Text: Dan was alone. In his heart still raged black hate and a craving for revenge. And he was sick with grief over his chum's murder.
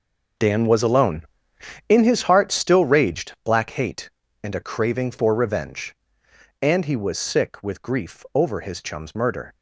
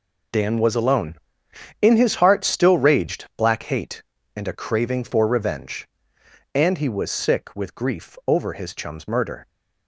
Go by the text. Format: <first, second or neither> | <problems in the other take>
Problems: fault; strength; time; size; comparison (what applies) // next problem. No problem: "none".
second | starts louder than the rest; noticeable; until 2.0 s; 6 dB